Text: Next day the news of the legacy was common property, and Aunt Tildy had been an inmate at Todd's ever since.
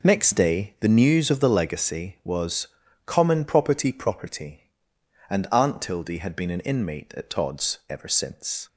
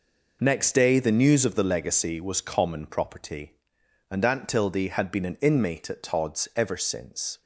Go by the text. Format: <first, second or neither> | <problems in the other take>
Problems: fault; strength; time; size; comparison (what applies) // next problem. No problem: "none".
second | pauses between "was" and "common"; at 2.6 s; 0.40 s long // says "property" twice; at 3.9 s